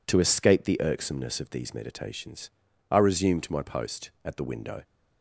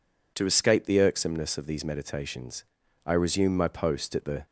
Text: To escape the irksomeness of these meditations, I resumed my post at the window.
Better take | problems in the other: first | stops before "window"; at 4.4 s

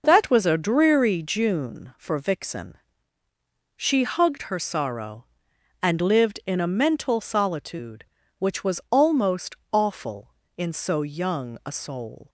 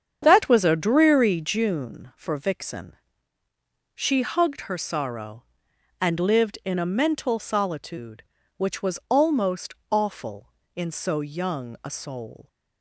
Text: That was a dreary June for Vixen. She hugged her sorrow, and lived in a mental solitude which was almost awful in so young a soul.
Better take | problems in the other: first | starts louder than the rest; strong; until 1.6 s; 7.5 dB // pauses between "almost" and "awful"; slight; at 9.7 s; 0.18 s long; slight in the first

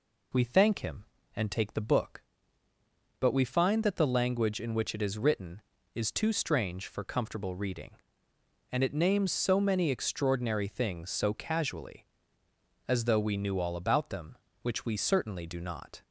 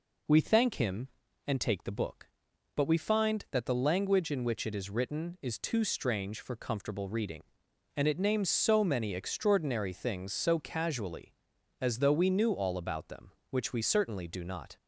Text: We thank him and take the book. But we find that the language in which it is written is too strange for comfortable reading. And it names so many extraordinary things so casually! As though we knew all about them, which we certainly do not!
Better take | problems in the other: neither | none

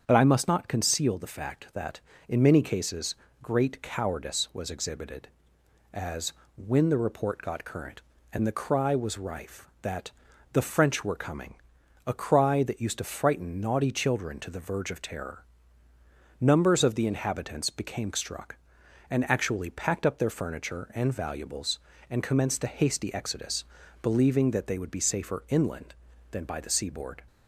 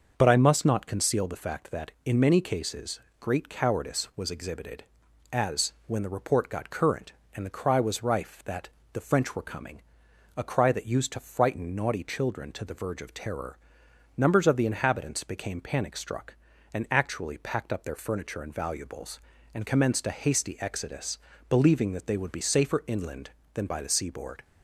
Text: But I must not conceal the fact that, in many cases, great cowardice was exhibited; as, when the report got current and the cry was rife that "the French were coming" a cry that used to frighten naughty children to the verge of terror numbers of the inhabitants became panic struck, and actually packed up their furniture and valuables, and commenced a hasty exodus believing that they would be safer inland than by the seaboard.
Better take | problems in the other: second | starts louder than the rest; strong; until 1.0 s; 7.5 dB; also in the second // pauses between "that" and "the"; at 10.1 s; 0.42 s long; slight in the second // pauses between "coming" and "a"; noticeable; at 11.5 s; 0.50 s long; noticeable in the second // pauses between "terror" and "numbers"; noticeable; at 15.4 s; 0.96 s long; noticeable in the second // skips "panic"; at 18.1 s // pauses between "exodus" and "believing"; at 23.6 s; 0.38 s long; slight in the second

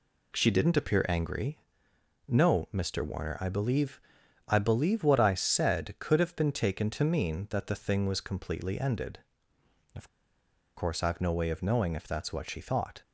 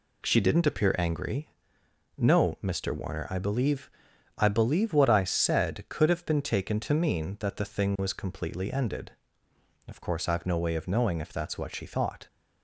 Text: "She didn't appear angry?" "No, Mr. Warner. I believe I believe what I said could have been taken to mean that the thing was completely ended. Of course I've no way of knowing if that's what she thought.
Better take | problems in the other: second | pauses between "believe" and "I"; noticeable; at 4.0 s; 0.46 s long; noticeable in the second // pauses between "Of" and "course"; noticeable; at 10.0 s; 0.68 s long

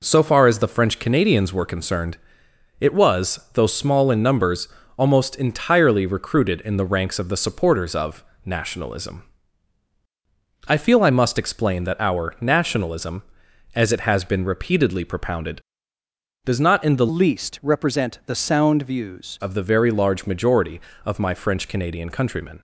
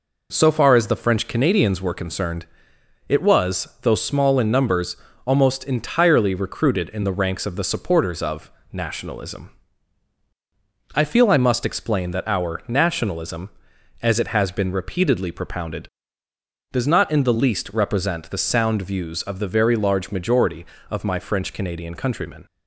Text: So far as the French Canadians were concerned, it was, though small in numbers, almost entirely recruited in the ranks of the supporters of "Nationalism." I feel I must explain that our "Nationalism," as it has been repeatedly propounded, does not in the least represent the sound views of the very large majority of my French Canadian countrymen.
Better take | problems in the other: second | pauses between "of" and "Nationalism"; slight; at 8.2 s; 0.20 s long; slight in the second // changes voice from "least" to "views"; from 17.0 to 19.3 s; 2.3 s long

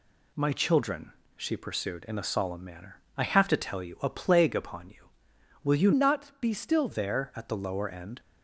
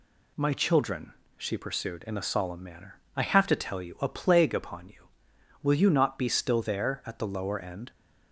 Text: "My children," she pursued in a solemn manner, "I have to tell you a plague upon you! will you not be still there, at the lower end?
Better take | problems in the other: second | changes voice from "not" to "still"; from 5.9 to 6.8 s; 0.9 s long

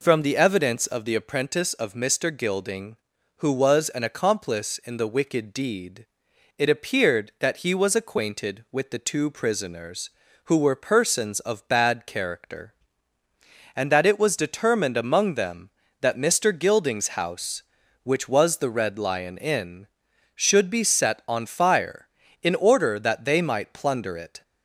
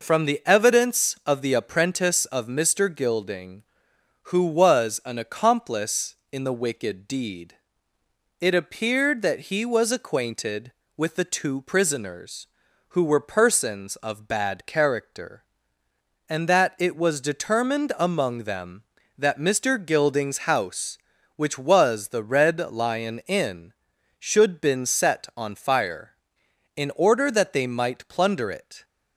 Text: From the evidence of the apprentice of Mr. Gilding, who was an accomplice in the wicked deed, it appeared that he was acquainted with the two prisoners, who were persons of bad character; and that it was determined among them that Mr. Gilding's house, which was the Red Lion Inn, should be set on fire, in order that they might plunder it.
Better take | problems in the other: first | says "been" for "be"; at 24.5 s

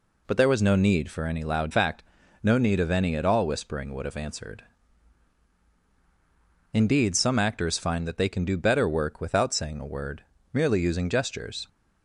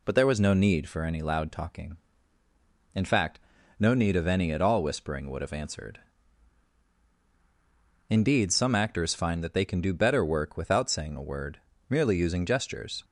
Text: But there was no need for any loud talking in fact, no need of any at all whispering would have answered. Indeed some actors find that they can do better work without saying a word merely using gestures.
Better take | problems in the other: second | skips "talking in"; at 1.7 s // pauses between "word" and "merely"; slight; at 10.2 s; 0.30 s long; slight in the second

